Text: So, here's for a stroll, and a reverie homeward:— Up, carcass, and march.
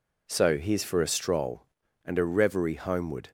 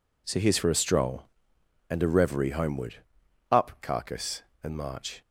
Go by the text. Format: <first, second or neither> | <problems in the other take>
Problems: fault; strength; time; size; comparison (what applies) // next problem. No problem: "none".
second | stops before "Up carcass and march"; at 3.2 s